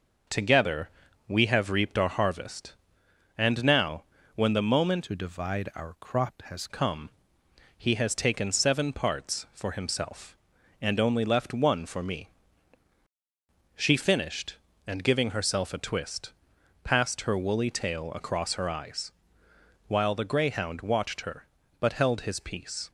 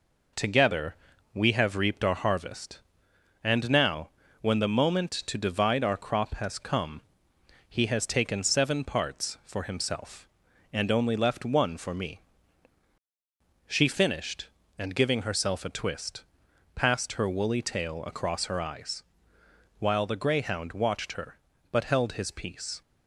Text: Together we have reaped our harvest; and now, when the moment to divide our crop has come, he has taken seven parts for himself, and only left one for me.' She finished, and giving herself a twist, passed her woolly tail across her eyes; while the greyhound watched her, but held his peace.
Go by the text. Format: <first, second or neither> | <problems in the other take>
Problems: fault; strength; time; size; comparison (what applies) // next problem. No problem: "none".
second | pauses between "Together" and "we"; at 0.8 s; 0.38 s long; also in the second // changes voice from "to" to "has"; from 5.0 to 6.6 s; 1.6 s long